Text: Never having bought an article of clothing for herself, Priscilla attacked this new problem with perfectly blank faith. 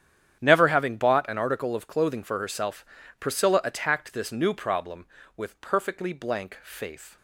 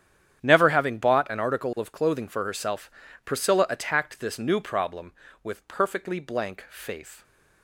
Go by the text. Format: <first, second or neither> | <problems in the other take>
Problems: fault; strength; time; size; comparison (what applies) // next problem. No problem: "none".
neither | starts louder than the rest; strong; the same in both